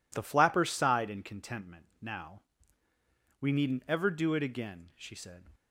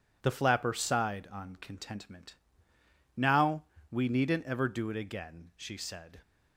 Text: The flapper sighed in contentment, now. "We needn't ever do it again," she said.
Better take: first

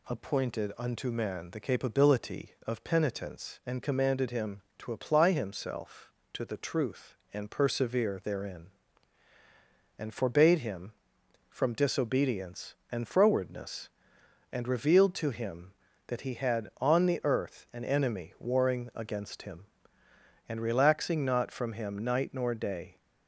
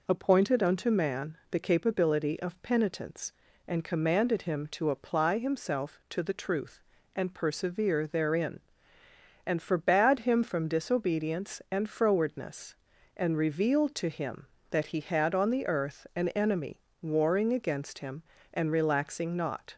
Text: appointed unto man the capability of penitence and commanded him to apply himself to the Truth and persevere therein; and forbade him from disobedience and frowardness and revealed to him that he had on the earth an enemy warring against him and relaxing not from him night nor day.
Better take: first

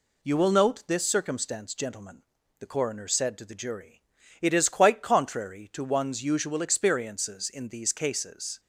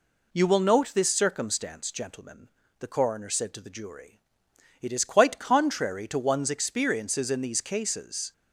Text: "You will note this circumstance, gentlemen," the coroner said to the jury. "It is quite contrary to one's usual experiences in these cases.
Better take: first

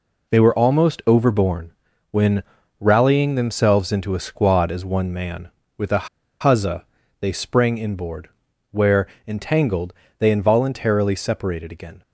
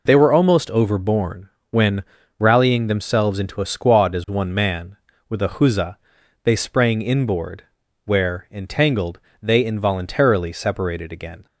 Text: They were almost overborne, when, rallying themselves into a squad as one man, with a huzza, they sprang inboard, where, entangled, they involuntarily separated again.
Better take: second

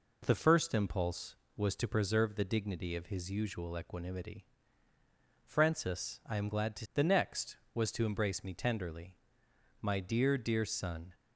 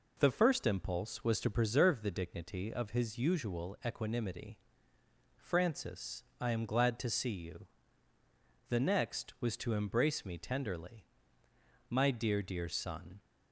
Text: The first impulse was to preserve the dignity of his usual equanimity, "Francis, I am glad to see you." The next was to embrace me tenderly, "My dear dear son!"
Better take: second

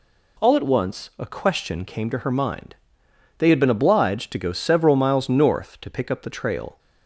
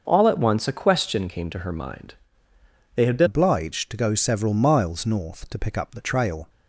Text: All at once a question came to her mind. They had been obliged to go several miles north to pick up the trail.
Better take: first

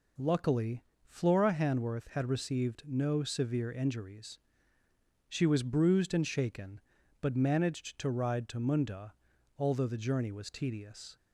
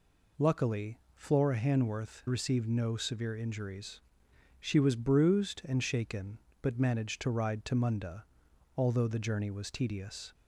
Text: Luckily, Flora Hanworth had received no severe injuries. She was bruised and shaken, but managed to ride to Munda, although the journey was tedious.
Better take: first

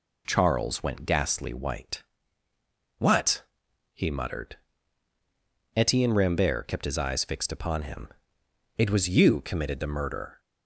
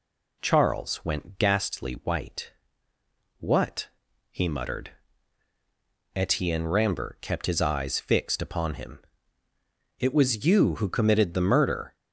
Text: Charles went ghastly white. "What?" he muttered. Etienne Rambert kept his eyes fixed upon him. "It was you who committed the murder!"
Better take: second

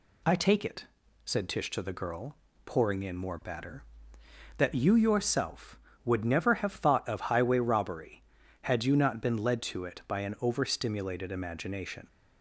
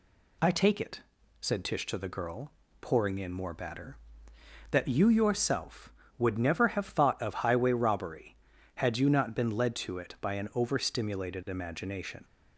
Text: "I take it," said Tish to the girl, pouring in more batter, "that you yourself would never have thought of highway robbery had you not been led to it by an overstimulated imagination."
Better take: neither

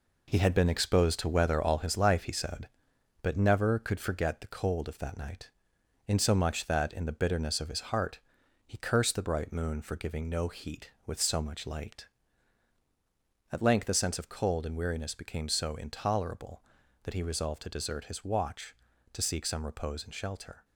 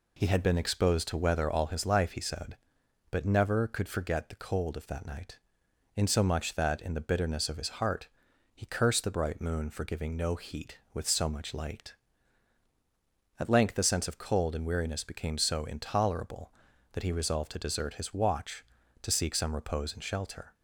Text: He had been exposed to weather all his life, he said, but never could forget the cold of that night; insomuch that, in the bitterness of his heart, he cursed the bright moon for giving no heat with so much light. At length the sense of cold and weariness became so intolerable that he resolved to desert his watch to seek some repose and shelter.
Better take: second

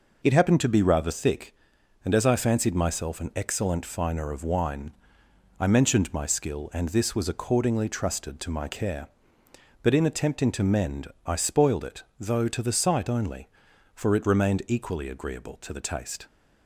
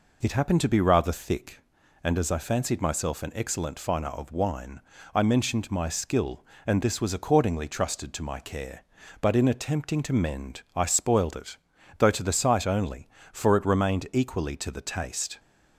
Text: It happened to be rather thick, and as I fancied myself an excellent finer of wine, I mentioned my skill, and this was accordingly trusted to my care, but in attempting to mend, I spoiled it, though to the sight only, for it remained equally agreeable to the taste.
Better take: first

